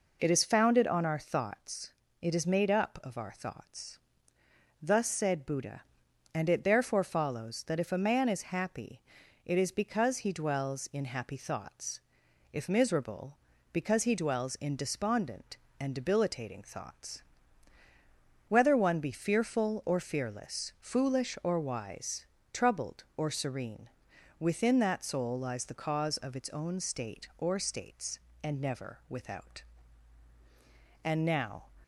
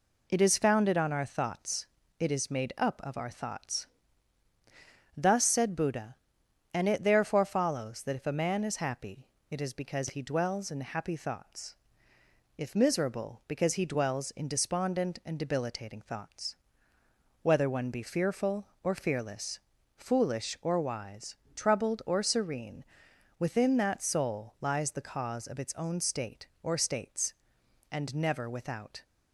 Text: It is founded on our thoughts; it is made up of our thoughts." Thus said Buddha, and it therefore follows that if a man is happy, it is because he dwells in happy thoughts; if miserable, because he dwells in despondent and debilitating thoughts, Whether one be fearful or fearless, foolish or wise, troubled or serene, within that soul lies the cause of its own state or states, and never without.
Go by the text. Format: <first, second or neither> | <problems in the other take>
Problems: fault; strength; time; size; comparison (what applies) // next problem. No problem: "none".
second | goes on to say "And now"; noticeable; from 31.0 s on; 0.66 s long